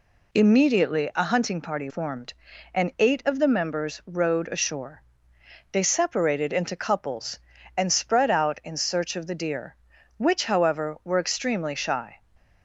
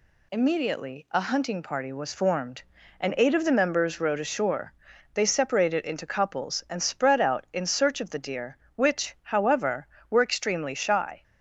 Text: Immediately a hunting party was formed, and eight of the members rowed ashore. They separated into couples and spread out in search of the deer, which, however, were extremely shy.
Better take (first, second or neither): second